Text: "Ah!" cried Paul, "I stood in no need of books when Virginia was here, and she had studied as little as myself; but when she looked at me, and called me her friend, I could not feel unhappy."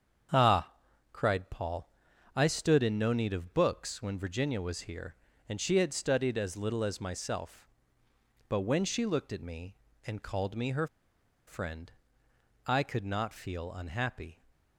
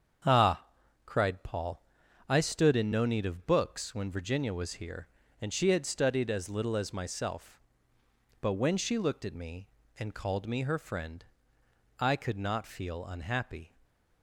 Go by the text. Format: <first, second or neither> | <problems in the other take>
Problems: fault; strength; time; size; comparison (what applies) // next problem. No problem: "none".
second | starts louder than the rest; strong; until 1.7 s; 7.5 dB; strong in the second // pauses between "her" and "friend"; noticeable; at 10.8 s; 0.61 s long